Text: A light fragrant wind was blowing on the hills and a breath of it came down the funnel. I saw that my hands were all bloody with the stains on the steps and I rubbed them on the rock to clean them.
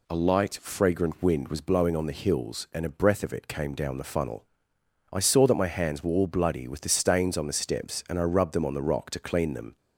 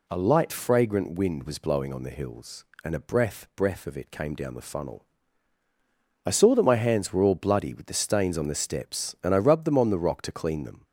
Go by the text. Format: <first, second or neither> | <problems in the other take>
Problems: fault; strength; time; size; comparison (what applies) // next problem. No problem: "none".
first | says "breath" twice; at 3.5 s